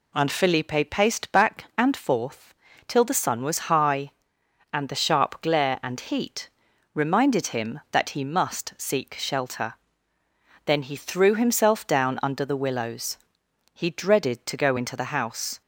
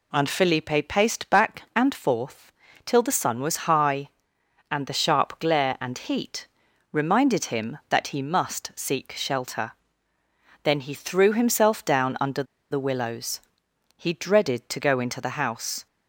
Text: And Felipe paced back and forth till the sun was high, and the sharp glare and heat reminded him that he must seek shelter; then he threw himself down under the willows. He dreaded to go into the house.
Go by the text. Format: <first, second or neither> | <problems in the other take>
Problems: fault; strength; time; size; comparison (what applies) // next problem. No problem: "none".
first | pauses between "forth" and "till"; slight; at 2.5 s; 0.34 s long; slight in the first // pauses between "heat" and "reminded"; at 6.4 s; 0.44 s long; also in the first // pauses between "under" and "the"; slight; at 12.4 s; 0.28 s long